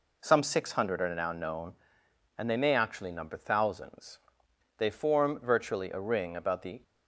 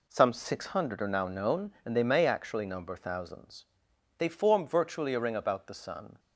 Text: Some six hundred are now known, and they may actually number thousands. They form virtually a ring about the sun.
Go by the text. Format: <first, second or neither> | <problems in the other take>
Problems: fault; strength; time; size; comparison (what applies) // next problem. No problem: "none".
second | stops before "sun"; at 6.8 s